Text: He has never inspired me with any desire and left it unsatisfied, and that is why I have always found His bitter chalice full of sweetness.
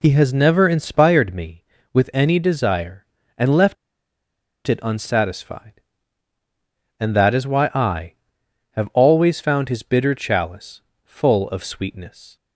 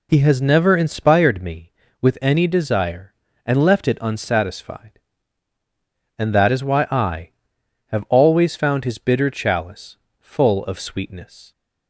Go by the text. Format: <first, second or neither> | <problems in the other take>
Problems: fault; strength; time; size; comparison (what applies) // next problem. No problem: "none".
second | pauses between "left" and "it"; noticeable; at 3.7 s; 0.92 s long // pauses between "chalice" and "full"; slight; at 10.8 s; 0.24 s long; slight in the second